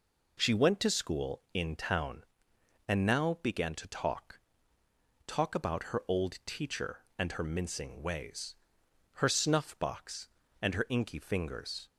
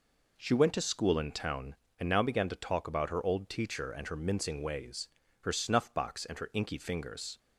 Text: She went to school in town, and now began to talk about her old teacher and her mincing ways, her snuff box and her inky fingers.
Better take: second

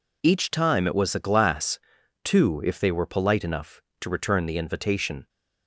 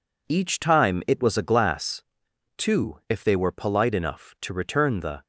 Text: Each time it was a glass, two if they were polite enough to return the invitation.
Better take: first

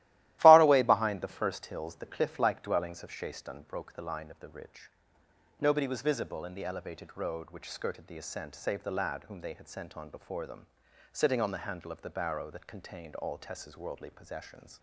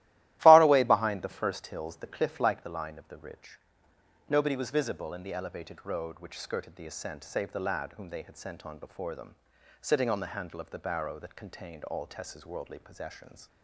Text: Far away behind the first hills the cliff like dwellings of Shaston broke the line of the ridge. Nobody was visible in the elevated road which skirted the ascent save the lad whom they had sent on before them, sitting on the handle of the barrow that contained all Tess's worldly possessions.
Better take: first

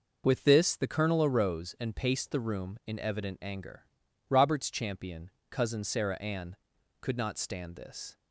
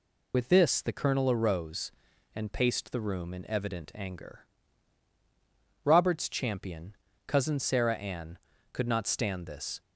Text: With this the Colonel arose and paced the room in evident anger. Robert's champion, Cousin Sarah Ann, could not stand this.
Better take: first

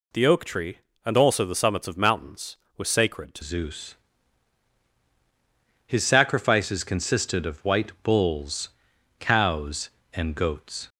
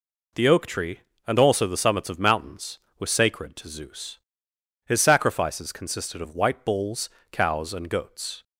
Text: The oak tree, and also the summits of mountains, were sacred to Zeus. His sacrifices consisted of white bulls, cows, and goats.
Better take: second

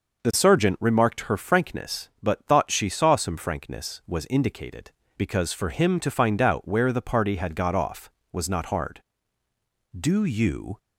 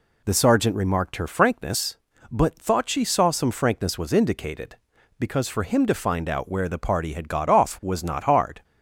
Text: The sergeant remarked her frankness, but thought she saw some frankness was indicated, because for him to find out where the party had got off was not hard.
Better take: second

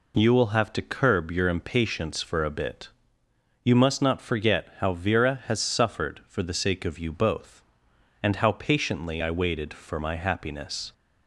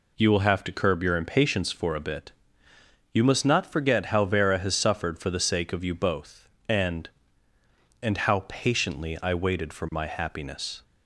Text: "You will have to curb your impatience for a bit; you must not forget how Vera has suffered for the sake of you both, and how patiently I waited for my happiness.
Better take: first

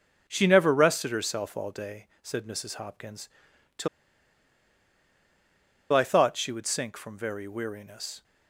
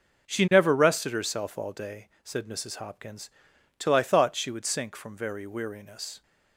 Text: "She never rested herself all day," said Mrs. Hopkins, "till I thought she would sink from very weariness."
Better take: second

